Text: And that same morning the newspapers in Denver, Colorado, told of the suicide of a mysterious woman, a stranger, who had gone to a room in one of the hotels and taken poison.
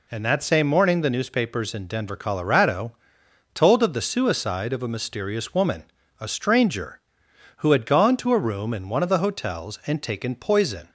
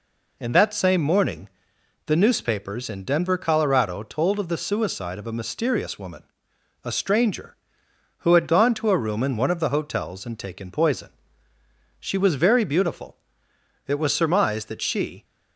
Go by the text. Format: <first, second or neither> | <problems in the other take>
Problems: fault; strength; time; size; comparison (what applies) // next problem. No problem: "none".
first | pauses between "morning" and "the"; noticeable; at 1.4 s; 0.58 s long // goes on to say "She was very beautiful it was surmised that she"; strong; from 11.9 s on; 3.2 s long